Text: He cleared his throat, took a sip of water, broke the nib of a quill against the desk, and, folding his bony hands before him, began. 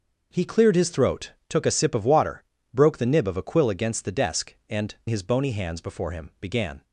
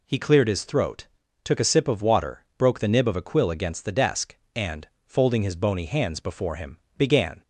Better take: second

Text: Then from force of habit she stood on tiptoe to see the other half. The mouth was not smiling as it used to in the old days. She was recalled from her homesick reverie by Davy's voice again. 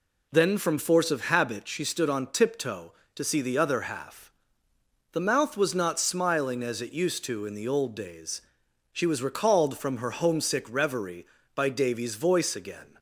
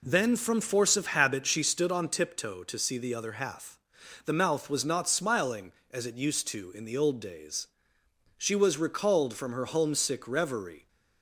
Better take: first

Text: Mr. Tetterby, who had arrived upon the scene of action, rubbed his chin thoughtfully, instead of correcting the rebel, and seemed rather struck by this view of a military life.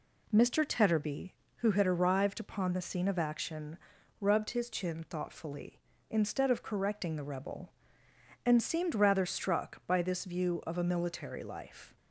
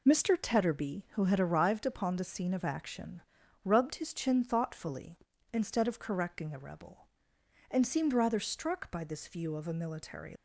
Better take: first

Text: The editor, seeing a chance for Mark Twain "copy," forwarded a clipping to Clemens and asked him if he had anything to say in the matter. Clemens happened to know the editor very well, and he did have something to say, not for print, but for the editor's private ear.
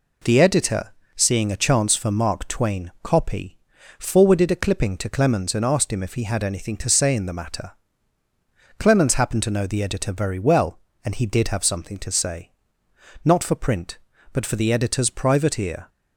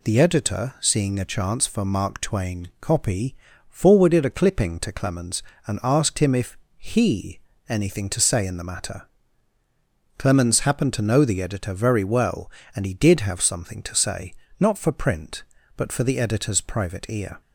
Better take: first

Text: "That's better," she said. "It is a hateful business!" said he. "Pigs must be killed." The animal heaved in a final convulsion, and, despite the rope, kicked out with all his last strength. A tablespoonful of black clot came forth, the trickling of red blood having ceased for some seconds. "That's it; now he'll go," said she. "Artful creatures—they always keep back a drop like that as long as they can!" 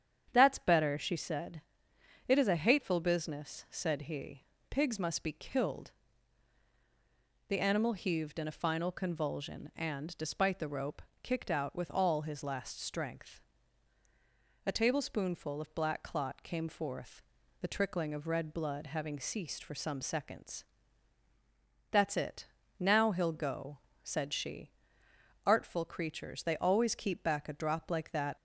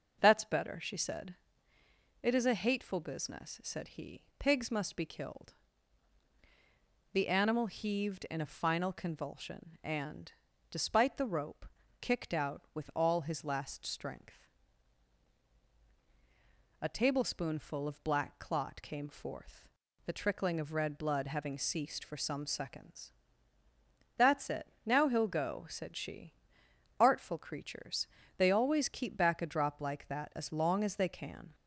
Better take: second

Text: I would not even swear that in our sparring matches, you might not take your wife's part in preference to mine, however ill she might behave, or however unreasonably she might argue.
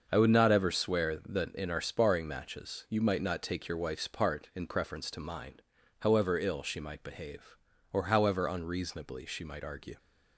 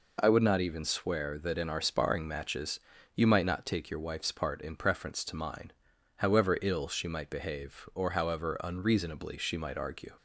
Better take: second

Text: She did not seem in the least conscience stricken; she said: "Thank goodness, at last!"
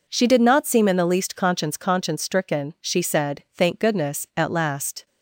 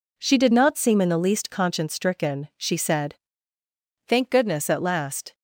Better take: second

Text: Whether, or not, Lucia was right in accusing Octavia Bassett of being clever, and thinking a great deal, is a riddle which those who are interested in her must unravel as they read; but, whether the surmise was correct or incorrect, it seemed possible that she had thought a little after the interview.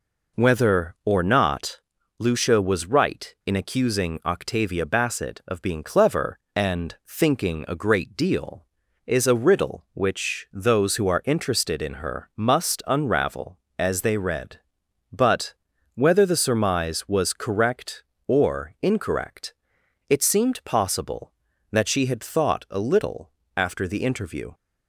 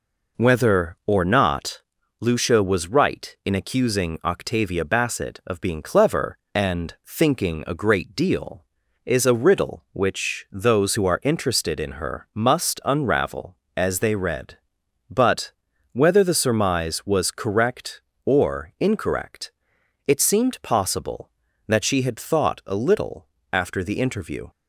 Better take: neither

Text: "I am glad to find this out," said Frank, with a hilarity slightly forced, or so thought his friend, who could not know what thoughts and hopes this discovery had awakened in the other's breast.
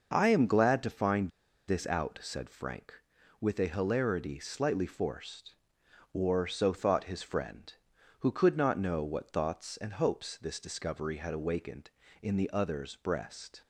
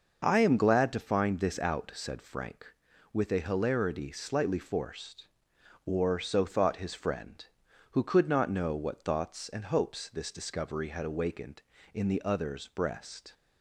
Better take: second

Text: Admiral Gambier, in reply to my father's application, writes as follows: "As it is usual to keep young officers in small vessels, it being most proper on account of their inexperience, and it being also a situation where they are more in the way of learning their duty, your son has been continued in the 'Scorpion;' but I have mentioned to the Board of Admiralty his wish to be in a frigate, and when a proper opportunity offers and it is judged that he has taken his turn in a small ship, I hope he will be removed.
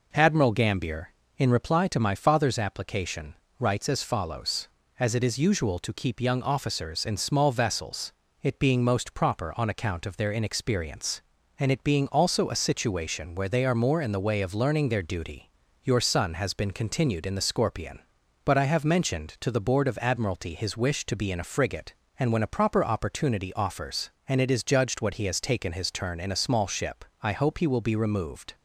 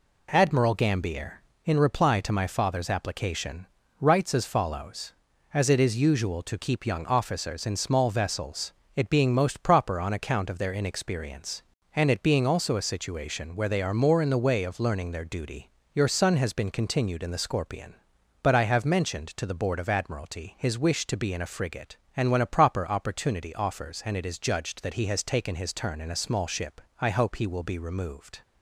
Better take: second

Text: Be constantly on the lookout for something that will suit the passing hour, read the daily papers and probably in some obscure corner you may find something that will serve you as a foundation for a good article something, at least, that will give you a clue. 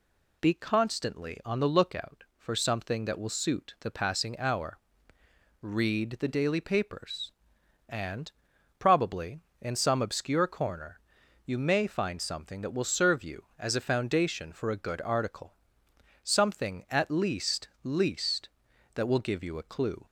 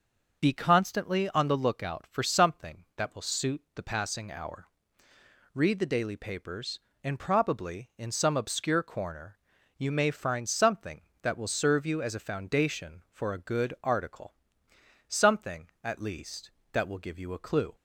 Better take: second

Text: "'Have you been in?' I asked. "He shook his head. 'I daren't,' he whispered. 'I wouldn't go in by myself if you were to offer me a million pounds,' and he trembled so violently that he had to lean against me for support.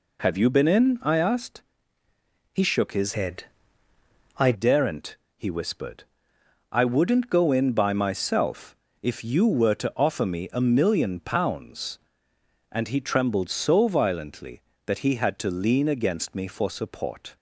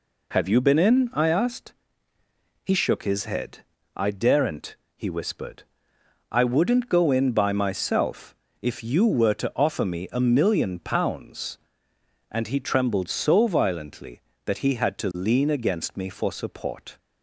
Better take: second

